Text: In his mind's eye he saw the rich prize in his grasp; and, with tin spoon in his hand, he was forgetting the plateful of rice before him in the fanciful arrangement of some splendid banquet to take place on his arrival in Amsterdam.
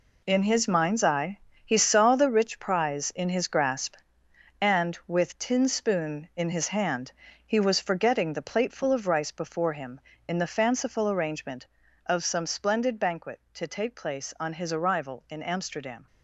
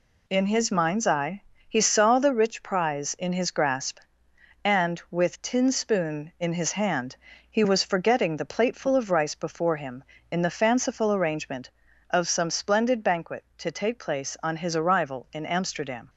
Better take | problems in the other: second | gets quieter; strong; throughout; 9 dB // pauses between "eye" and "he"; slight; at 1.4 s; 0.24 s long; slight in the second

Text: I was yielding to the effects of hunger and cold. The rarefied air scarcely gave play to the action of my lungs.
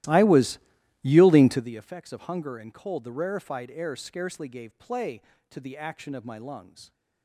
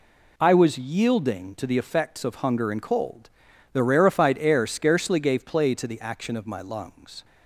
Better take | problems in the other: second | starts louder than the rest; strong; until 1.7 s; 15.5 dB // pauses between "was" and "yielding"; at 0.5 s; 0.44 s long

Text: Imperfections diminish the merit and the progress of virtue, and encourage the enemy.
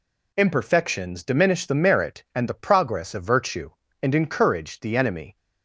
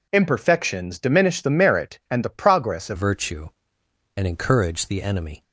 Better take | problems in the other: first | changes voice at "virtue"; from 2.9 s on; 2.5 s long

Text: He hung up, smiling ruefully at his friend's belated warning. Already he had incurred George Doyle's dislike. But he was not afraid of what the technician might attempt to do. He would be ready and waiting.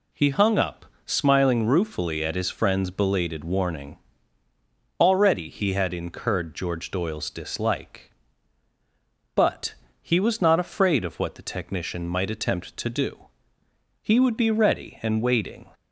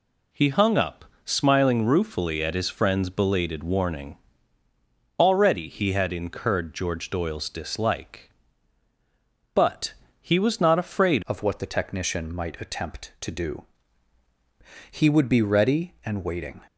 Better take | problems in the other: first | pauses between "But" and "he"; slight; at 9.9 s; 0.28 s long; slight in the first // changes voice at "of"; from 11.2 s on; 5.4 s long

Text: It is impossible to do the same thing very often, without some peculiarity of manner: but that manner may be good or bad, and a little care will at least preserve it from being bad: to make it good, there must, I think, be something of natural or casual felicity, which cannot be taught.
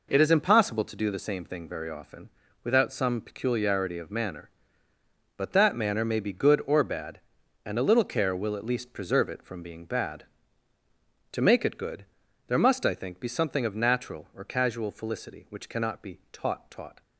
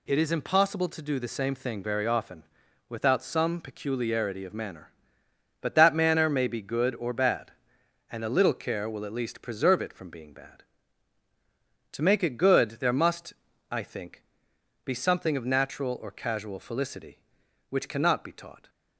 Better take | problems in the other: second | says "taught" twice; at 16.7 s

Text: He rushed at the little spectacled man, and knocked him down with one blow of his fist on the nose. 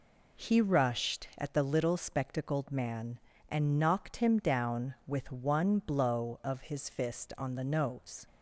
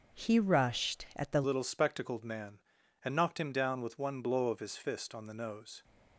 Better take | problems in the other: first | starts louder than the rest; until 1.2 s; 6.5 dB // changes voice at "little"; from 1.4 s on; 4.4 s long

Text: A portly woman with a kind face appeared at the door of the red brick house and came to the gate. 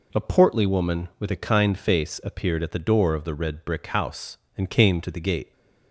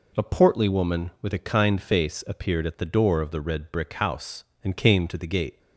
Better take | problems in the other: neither | none

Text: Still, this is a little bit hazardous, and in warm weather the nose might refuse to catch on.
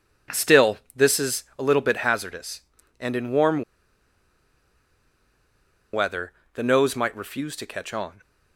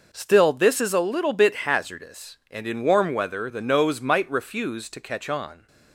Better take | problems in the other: second | pauses between "warm" and "weather"; strong; at 3.6 s; 2.3 s long // pauses between "weather" and "the"; slight; at 6.3 s; 0.22 s long

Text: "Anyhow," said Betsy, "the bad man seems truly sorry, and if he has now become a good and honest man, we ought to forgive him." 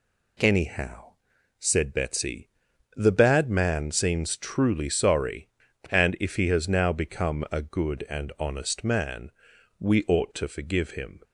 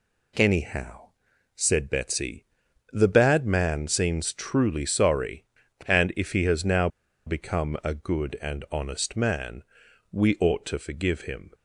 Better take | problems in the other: first | pauses between "now" and "become"; at 6.8 s; 0.38 s long

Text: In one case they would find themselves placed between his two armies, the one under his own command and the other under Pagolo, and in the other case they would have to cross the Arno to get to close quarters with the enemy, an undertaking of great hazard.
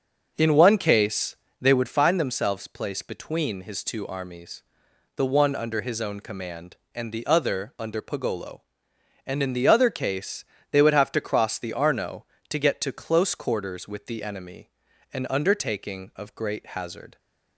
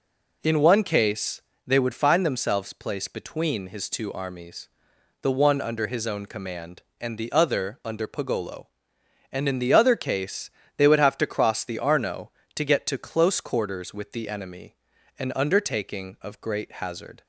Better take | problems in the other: second | starts louder than the rest; noticeable; until 2.0 s; 6 dB // pauses between "case" and "they"; slight; at 1.3 s; 0.26 s long; slight in the second // pauses between "case" and "they"; slight; at 10.4 s; 0.28 s long; slight in the second

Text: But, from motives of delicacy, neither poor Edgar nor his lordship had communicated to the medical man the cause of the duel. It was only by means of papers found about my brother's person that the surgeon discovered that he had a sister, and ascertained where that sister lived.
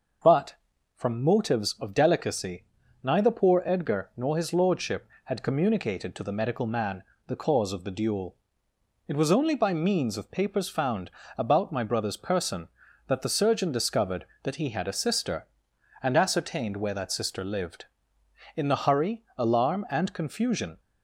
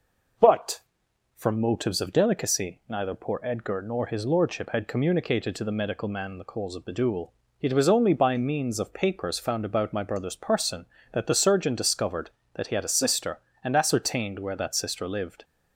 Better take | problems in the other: second | starts louder than the rest; noticeable; until 1.6 s; 6 dB // pauses between "man" and "the"; slight; at 7.0 s; 0.24 s long // pauses between "found" and "about"; slight; at 11.0 s; 0.28 s long // goes on to say "In the hurry alarm and confusion"; strong; from 18.5 s on; 2.2 s long

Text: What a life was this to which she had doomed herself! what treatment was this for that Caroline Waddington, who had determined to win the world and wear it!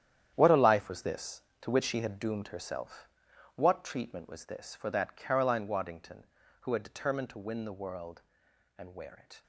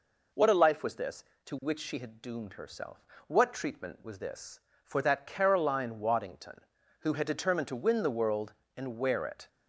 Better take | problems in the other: second | gets quieter; strong; throughout; 11.5 dB

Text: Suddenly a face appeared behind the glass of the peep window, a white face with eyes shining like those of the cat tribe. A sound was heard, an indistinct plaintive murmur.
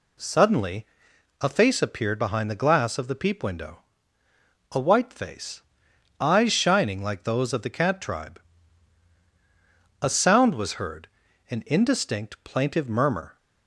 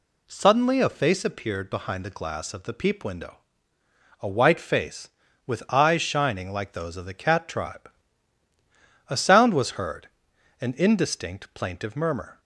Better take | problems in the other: second | pauses between "Suddenly" and "a"; noticeable; at 0.8 s; 0.56 s long // skips "with"; at 5.9 s

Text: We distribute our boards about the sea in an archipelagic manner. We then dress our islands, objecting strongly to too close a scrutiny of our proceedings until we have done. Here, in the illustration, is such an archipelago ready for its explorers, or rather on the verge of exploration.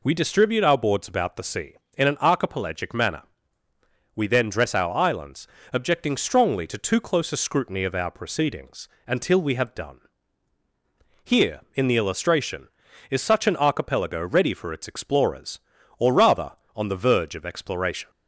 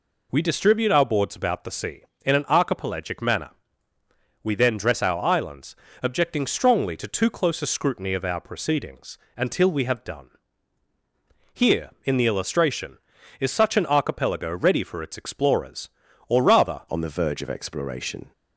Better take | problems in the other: first | pauses between "proceedings" and "until"; slight; at 9.1 s; 0.18 s long; slight in the first // changes voice at "on"; from 16.8 s on; 1.5 s long

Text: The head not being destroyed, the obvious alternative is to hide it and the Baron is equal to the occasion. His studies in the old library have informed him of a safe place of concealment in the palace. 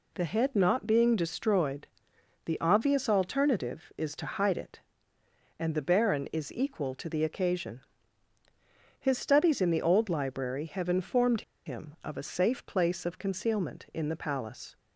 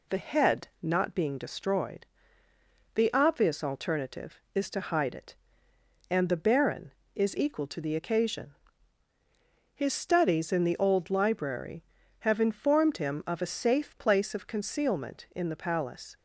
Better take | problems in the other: second | pauses between "informed" and "him"; slight; at 11.4 s; 0.24 s long

